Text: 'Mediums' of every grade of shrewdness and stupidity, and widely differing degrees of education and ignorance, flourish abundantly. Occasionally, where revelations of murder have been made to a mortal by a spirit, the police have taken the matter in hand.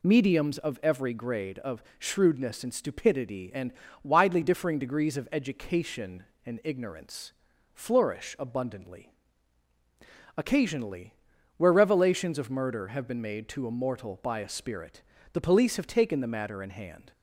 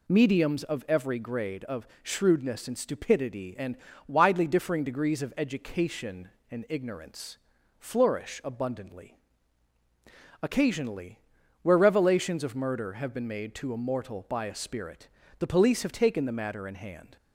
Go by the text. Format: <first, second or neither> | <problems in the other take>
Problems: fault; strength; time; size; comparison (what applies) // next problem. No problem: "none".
neither | pauses between "of" and "shrewdness"; slight; the same in both // pauses between "and" and "widely"; slight; the same in both